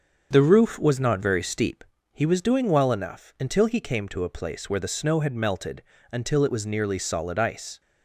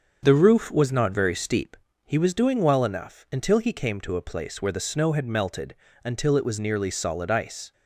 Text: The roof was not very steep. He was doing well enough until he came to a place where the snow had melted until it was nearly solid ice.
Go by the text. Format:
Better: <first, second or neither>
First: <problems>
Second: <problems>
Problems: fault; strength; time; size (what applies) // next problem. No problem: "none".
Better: neither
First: starts louder than the rest; until 1.3 s; 7 dB // pauses between "melted" and "until"; slight; at 5.8 s; 0.28 s long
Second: starts louder than the rest; until 1.2 s; 6.5 dB // pauses between "melted" and "until"; slight; at 5.7 s; 0.28 s long